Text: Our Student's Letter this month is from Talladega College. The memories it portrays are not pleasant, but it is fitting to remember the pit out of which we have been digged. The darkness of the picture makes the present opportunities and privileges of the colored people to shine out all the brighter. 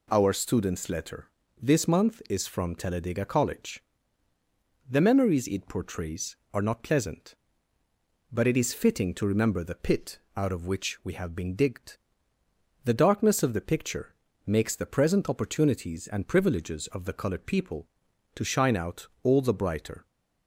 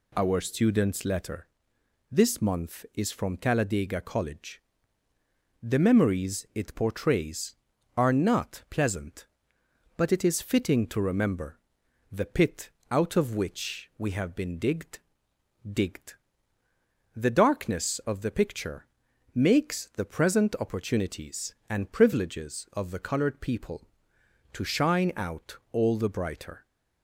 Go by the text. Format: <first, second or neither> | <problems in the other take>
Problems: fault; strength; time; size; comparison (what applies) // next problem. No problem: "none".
first | pauses between "Letter" and "this"; noticeable; at 1.4 s; 0.64 s long; slight in the first // pauses between "remember" and "the"; noticeable; at 11.5 s; 0.54 s long // pauses between "pit" and "out"; slight; at 12.6 s; 0.22 s long; slight in the first // says "digged" twice; at 15.7 s // pauses between "picture" and "makes"; noticeable; at 18.8 s; 0.48 s long; slight in the first